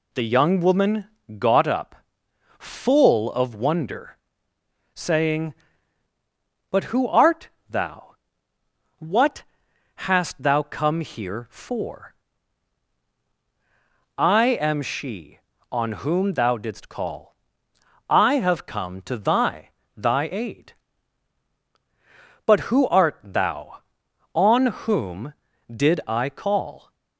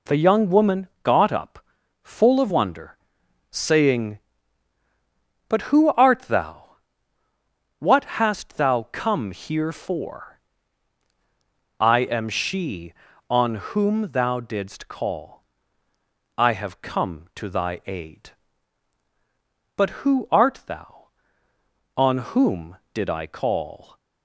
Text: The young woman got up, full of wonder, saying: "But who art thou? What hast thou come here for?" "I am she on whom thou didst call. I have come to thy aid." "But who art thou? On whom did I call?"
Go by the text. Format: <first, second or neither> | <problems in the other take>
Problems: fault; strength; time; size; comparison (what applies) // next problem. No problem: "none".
second | pauses between "woman" and "got"; slight; at 1.0 s; 0.30 s long; slight in the second // pauses between "art" and "thou"; slight; at 7.4 s; 0.22 s long // pauses between "What" and "hast"; noticeable; at 9.4 s; 0.64 s long; slight in the second // says "thy" twice; at 19.9 s